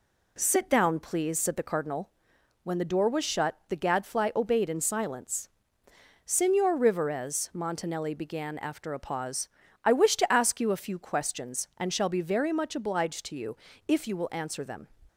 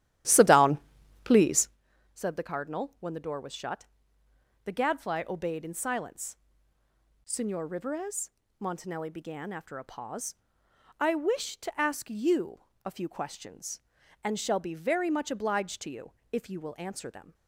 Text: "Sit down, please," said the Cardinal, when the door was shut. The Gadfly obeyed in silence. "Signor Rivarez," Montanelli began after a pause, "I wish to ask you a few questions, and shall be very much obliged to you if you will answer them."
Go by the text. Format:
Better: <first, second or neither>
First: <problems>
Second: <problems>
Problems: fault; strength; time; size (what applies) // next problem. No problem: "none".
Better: first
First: pauses between "you" and "if"; slight; at 13.5 s; 0.30 s long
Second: starts louder than the rest; strong; until 1.8 s; 13 dB // pauses between "you" and "a"; slight; at 12.6 s; 0.22 s long // pauses between "you" and "if"; slight; at 16.0 s; 0.22 s long